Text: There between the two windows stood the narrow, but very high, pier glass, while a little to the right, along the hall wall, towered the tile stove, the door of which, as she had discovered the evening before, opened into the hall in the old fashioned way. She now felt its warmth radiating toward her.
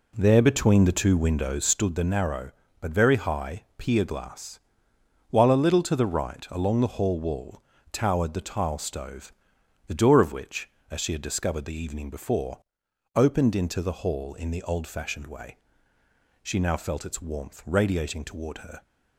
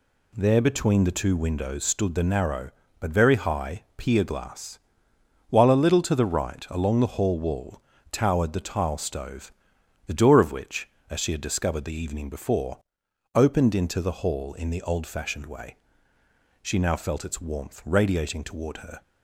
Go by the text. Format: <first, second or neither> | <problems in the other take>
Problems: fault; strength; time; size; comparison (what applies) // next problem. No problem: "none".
second | starts louder than the rest; slight; until 2.0 s; 2.5 dB